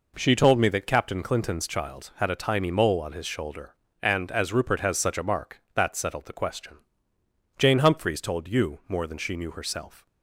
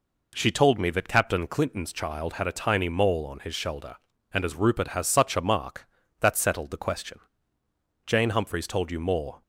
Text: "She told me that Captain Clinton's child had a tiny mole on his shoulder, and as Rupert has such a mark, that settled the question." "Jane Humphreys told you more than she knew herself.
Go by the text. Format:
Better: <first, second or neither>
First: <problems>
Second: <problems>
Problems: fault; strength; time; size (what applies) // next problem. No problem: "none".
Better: first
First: none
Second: stops before "than she knew herself"; at 9.4 s